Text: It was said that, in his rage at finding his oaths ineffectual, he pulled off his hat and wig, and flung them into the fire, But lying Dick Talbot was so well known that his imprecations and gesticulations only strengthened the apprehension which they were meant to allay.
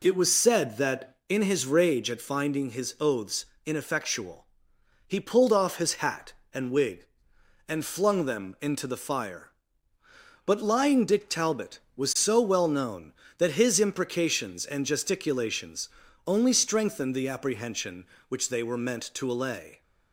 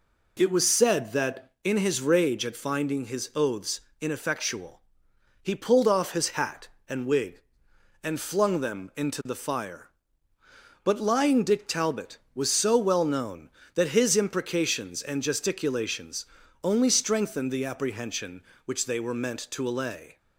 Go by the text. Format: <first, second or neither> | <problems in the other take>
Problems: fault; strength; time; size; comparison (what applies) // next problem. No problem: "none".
neither | pauses between "oaths" and "ineffectual"; slight; the same in both // pauses between "gesticulations" and "only"; the same in both